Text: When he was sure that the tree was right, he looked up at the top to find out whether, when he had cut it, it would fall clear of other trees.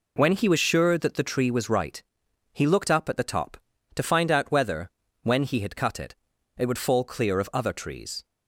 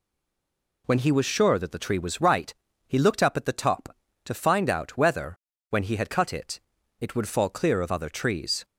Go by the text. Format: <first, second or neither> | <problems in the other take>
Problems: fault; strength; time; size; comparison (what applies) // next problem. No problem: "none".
first | stays silent before the first word; slight; until 0.8 s; 0.8 s long